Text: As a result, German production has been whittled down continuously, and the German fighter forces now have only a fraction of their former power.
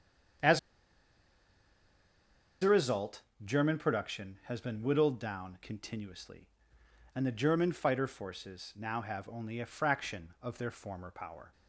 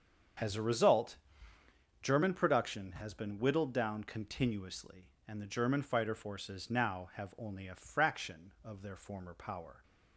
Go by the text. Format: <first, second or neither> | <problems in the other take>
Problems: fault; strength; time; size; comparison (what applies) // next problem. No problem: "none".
second | starts louder than the rest; strong; until 3.6 s; 8 dB; strong in the second // pauses between "As" and "a"; strong; at 0.5 s; 2.0 s long